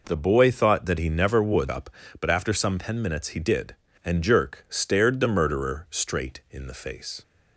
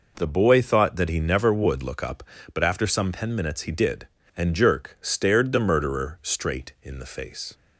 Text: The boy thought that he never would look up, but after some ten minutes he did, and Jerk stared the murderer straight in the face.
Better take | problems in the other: second | skips "look"; at 1.6 s

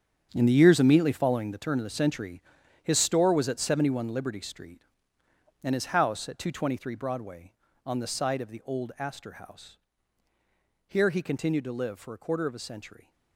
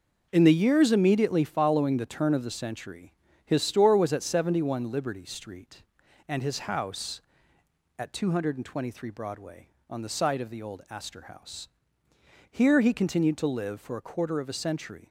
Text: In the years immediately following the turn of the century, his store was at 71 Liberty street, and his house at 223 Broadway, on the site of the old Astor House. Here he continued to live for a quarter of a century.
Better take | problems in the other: second | gets quieter; strong; throughout; 13 dB

